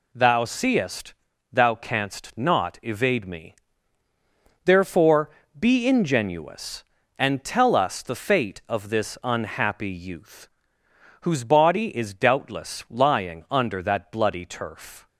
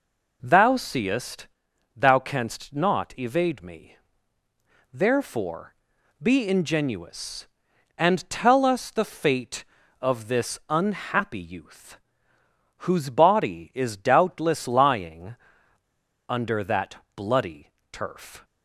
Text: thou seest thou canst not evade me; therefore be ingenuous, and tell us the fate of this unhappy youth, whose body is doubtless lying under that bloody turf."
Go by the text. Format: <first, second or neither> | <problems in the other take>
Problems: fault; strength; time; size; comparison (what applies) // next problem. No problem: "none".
first | pauses between "seest" and "thou"; noticeable; at 1.4 s; 0.48 s long; also in the first // pauses between "therefore" and "be"; noticeable; at 5.7 s; 0.48 s long; slight in the first // pauses between "lying" and "under"; noticeable; at 15.3 s; 0.93 s long // pauses between "that" and "bloody"; slight; at 16.9 s; 0.18 s long // pauses between "bloody" and "turf"; slight; at 17.7 s; 0.22 s long